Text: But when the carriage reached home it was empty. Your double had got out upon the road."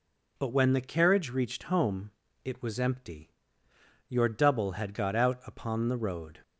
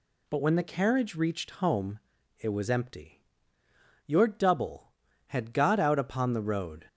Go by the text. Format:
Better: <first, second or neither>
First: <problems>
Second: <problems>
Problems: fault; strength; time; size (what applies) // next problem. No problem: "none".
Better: neither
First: pauses between "home" and "it"; slight; at 2.1 s; 0.34 s long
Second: pauses between "home" and "it"; at 2.0 s; 0.40 s long